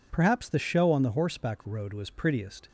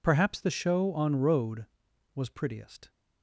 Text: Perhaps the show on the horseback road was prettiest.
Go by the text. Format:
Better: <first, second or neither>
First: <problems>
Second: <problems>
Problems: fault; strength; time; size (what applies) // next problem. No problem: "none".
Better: first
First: none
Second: skips "the horseback"; at 1.1 s